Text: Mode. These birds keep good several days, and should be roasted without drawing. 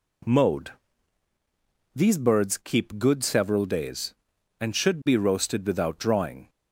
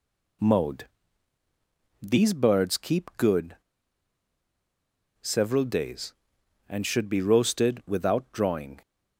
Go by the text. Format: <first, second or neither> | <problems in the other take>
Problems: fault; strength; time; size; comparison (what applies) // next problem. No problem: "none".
first | pauses between "good" and "several"; strong; at 3.5 s; 1.6 s long